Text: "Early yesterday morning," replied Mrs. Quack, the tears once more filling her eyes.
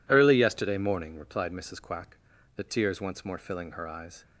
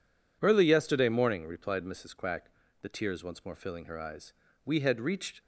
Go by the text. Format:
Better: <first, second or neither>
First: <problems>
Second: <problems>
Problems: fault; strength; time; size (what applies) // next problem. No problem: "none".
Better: first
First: none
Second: goes on to say "We had reached"; noticeable; from 4.6 s on; 0.76 s long